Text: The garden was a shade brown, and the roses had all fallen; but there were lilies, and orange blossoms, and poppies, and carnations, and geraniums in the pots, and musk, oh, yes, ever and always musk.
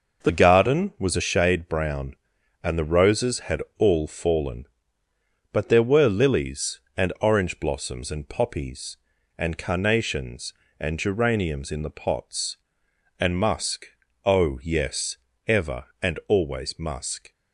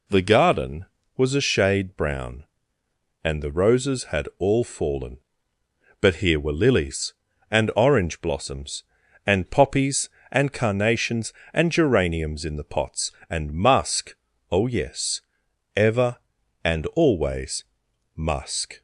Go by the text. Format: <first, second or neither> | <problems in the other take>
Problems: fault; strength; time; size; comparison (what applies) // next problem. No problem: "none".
first | says "here" for "there"; at 6.1 s // pauses between "always" and "musk"; noticeable; at 17.6 s; 0.49 s long